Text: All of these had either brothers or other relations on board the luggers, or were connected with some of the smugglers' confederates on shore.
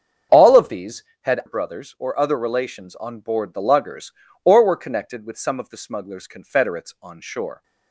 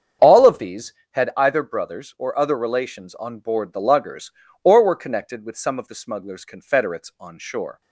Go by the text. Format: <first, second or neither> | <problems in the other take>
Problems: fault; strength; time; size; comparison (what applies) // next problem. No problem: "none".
second | starts louder than the rest; strong; until 1.5 s; 7.5 dB; strong in the second // skips "either"; at 1.4 s